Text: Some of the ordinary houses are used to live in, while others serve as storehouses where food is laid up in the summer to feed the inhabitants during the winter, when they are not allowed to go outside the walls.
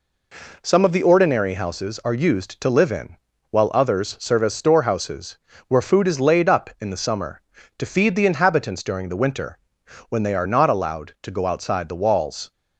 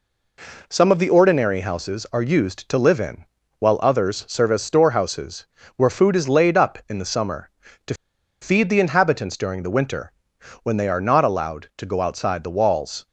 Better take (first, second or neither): first